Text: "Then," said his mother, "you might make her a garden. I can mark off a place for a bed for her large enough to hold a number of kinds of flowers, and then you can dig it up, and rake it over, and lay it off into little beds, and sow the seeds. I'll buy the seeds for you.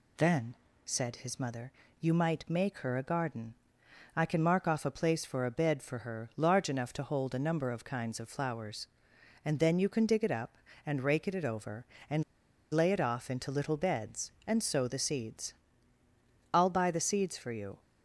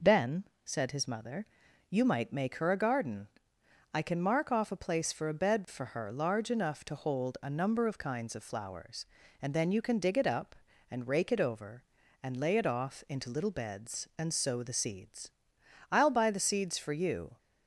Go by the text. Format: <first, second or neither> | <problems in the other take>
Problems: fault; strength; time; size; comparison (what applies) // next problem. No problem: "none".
second | pauses between "and" and "lay"; noticeable; at 12.2 s; 0.48 s long